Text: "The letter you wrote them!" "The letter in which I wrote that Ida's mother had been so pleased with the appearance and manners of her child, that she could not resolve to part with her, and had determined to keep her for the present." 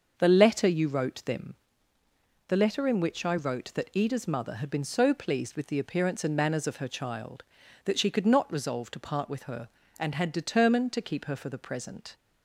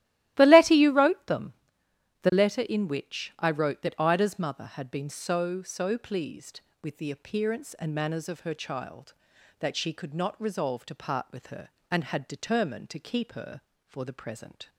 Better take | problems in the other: first | starts louder than the rest; strong; until 1.3 s; 15 dB; also in the first // says "so" twice; at 5.6 s

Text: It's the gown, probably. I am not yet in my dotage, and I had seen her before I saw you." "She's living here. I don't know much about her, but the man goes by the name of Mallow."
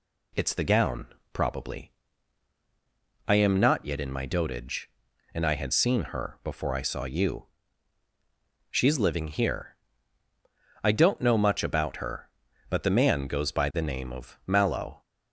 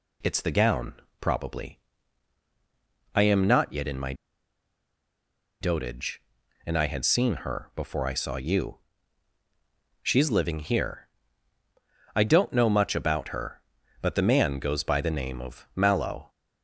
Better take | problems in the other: first | pauses between "my" and "dotage"; strong; at 4.1 s; 1.4 s long

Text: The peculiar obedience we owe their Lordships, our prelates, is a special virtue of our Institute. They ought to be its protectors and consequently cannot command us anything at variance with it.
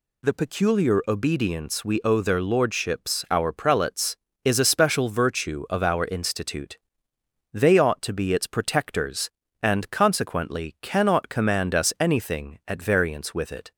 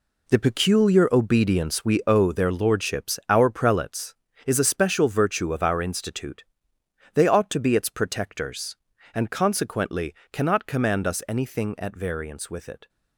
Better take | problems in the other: first | gets quieter; strong; throughout; 10 dB // pauses between "consequently" and "cannot"; slight; at 10.1 s; 0.20 s long

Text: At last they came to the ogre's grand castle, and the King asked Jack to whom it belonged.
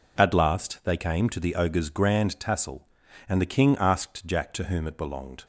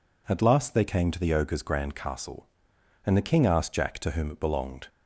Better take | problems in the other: second | says "tassel" for "castle"; at 2.3 s

